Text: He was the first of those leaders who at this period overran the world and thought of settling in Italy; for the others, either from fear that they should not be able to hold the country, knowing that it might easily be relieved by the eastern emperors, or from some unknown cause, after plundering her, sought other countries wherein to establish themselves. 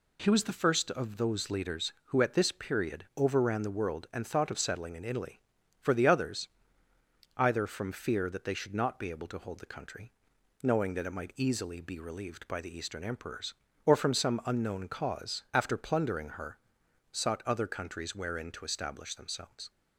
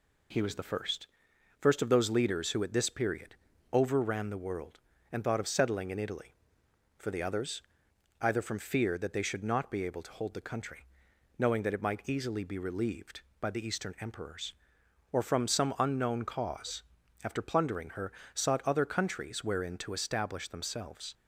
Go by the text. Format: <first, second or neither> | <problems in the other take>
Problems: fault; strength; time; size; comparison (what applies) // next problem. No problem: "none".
first | says "first" twice; at 1.5 s // pauses between "period" and "overran"; at 3.3 s; 0.38 s long